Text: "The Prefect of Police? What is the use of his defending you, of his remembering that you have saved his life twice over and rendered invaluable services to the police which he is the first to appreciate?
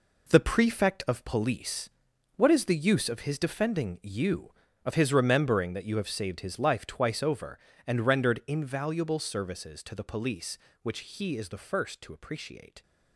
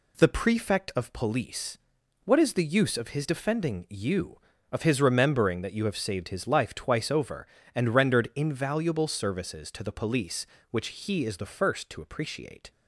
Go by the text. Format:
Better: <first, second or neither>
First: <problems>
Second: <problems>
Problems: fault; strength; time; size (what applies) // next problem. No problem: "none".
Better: second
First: gets quieter; strong; throughout; 10 dB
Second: none